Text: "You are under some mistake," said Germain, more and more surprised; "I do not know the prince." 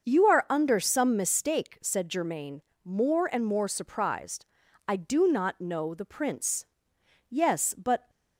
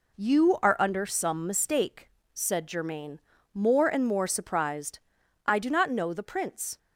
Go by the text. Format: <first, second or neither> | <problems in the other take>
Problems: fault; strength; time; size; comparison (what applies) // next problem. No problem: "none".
second | starts louder than the rest; until 1.1 s; 6.5 dB // goes on to say "Yes but"; noticeable; from 7.2 s on; 0.80 s long